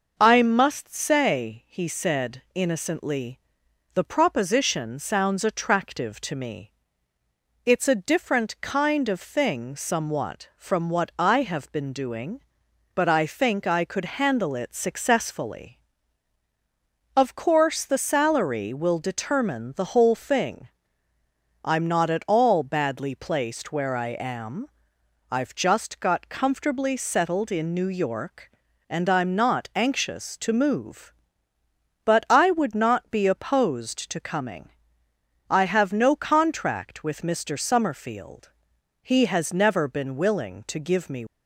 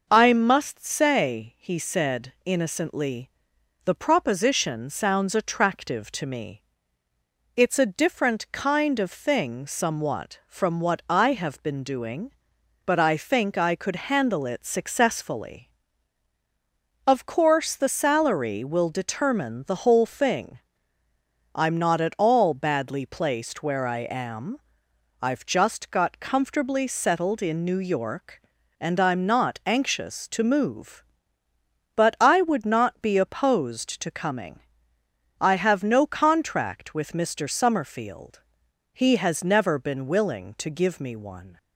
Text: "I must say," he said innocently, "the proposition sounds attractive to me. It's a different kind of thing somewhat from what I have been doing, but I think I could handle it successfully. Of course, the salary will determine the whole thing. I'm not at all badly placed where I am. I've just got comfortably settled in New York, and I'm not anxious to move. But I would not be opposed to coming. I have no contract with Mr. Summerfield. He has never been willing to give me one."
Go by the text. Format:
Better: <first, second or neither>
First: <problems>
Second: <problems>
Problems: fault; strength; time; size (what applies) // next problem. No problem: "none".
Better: second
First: stops before "one"; at 41.2 s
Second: none